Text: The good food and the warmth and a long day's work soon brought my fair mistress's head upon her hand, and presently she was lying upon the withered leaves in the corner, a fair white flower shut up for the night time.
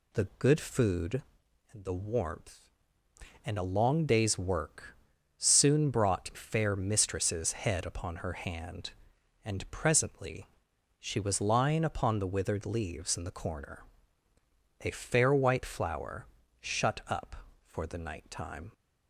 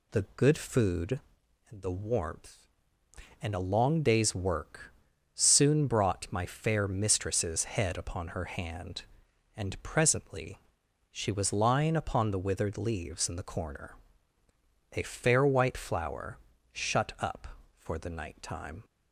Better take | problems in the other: second | pauses between "work" and "soon"; at 4.9 s; 0.42 s long; also in the second // skips "my"; at 6.3 s // pauses between "presently" and "she"; noticeable; at 10.4 s; 0.52 s long; noticeable in the second // pauses between "flower" and "shut"; slight; at 16.2 s; 0.34 s long; slight in the second

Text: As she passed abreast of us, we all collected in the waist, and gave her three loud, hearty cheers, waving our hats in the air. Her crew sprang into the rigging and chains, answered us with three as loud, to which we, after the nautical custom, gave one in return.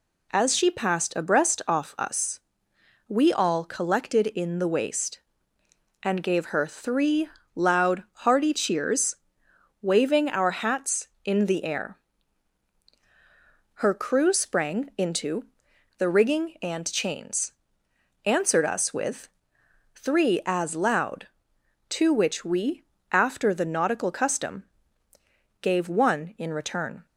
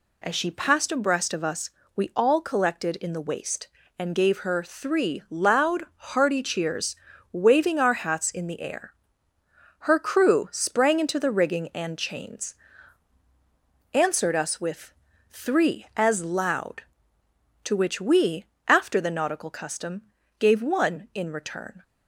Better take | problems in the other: second | says "off" for "of"; at 1.6 s // pauses between "three" and "loud"; slight; at 7.2 s; 0.24 s long // pauses between "into" and "the"; noticeable; at 15.4 s; 0.52 s long // pauses between "with" and "three"; noticeable; at 19.2 s; 0.66 s long; slight in the second

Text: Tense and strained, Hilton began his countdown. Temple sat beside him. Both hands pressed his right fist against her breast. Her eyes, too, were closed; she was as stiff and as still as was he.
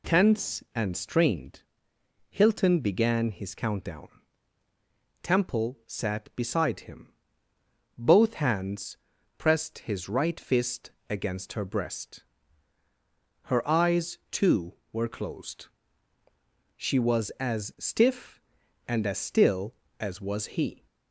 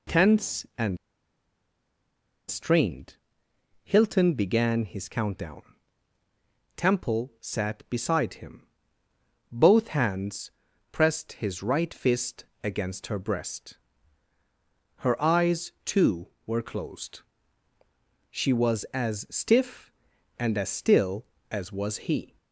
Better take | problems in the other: first | pauses between "and" and "strained"; strong; at 0.9 s; 1.5 s long // pauses between "hands" and "pressed"; at 10.5 s; 0.42 s long; also in the first // pauses between "fist" and "against"; slight; at 12.4 s; 0.18 s long; slight in the first

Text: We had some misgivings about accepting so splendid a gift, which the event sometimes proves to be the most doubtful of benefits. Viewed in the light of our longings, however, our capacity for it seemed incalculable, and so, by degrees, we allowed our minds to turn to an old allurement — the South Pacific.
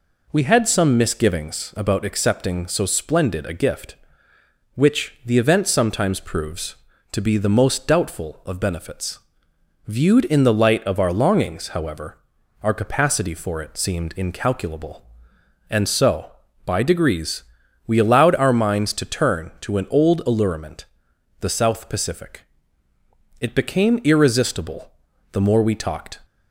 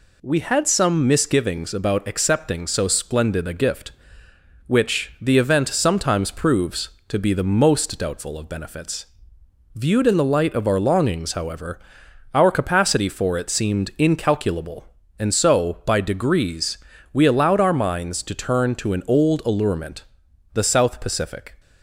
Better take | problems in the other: second | goes on to say "It became irresistible the more we talked"; strong; from 23.4 s on; 2.7 s long

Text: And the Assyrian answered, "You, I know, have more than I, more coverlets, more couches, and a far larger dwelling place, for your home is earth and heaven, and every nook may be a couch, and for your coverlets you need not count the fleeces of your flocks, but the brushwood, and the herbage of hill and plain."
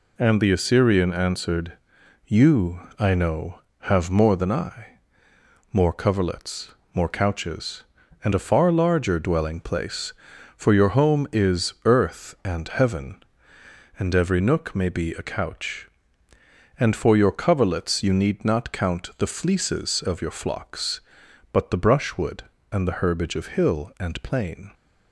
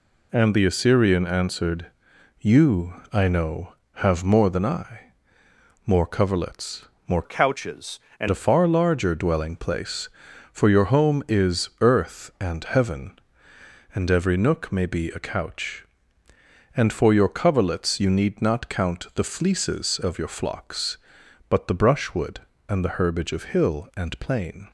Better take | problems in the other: first | changes voice from "couches" to "and"; from 7.2 to 8.2 s; 1.0 s long

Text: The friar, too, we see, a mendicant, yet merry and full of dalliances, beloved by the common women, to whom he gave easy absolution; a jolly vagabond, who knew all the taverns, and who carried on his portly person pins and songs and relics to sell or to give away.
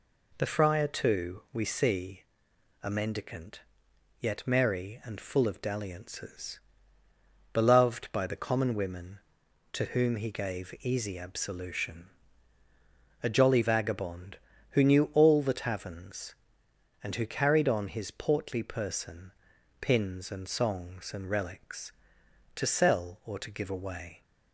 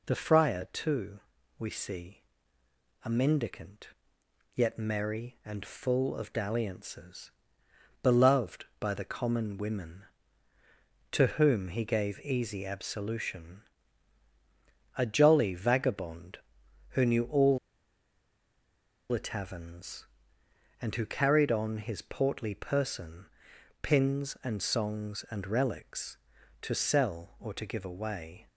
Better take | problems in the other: first | pauses between "all" and "the"; strong; at 17.5 s; 1.5 s long // pauses between "person" and "pins"; noticeable; at 23.2 s; 0.56 s long; noticeable in the first

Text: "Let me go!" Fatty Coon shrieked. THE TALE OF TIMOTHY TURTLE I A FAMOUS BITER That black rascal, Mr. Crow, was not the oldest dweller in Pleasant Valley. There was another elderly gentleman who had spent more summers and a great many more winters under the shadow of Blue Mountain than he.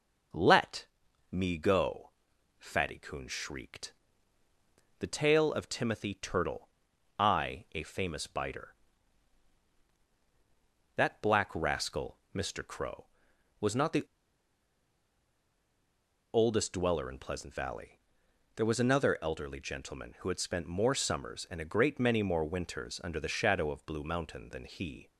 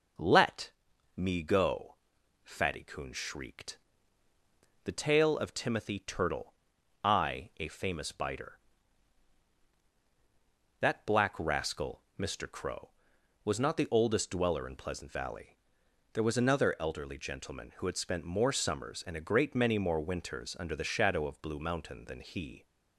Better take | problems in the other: second | pauses between "Let" and "me"; at 0.8 s; 0.42 s long; also in the second // pauses between "TURTLE" and "I"; noticeable; at 6.6 s; 0.50 s long; noticeable in the second // pauses between "the" and "oldest"; strong; at 14.0 s; 2.2 s long

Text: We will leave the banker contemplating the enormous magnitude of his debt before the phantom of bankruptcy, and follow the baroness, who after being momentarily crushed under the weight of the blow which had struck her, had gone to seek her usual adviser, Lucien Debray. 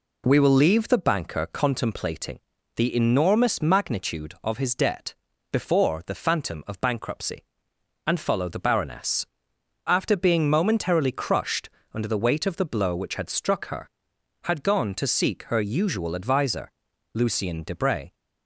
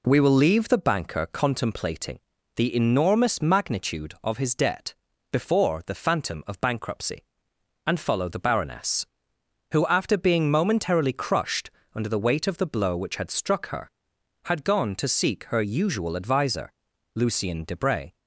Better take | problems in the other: second | pauses between "contemplating" and "the"; at 2.3 s; 0.38 s long; also in the second // pauses between "debt" and "before"; at 5.1 s; 0.38 s long; also in the second // skips "who"; at 9.5 s // pauses between "crushed" and "under"; slight; at 11.6 s; 0.24 s long; slight in the second

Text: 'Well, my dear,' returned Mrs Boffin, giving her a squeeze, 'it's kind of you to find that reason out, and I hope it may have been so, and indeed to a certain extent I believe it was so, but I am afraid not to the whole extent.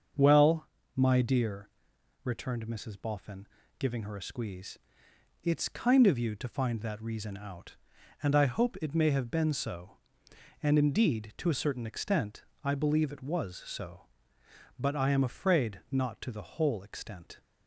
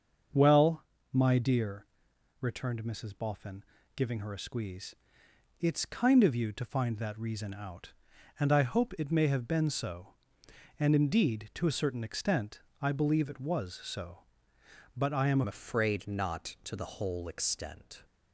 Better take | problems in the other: first | starts louder than the rest; until 1.6 s; 6.5 dB; also in the first // pauses between "extent" and "I"; slight; at 12.6 s; 0.18 s long; slight in the first // changes voice at "afraid"; from 15.4 s on; 2.6 s long

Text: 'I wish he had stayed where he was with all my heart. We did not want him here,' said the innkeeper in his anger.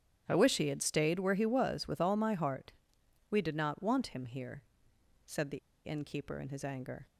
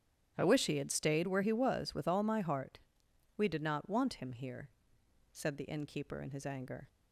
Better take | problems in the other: second | starts louder than the rest; strong; until 1.2 s; 8.5 dB; strong in the second // pauses between "the" and "innkeeper"; slight; at 5.5 s; 0.26 s long

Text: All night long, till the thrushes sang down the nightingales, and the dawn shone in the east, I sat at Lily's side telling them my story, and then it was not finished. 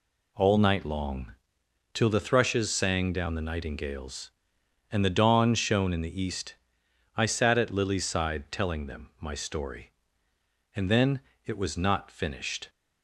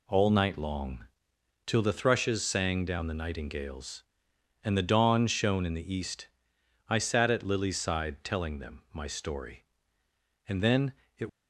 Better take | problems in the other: first | pauses between "then" and "it"; slight; at 10.9 s; 0.26 s long; slight in the first // stops before "was not finished"; at 11.2 s

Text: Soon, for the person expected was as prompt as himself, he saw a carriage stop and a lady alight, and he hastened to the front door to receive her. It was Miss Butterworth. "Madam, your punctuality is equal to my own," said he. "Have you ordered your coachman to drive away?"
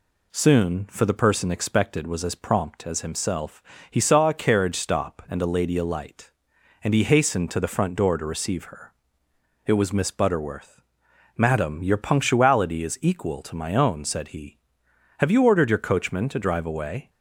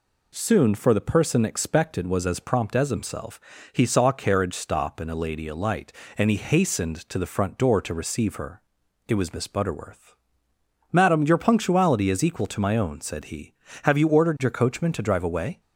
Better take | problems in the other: neither | none

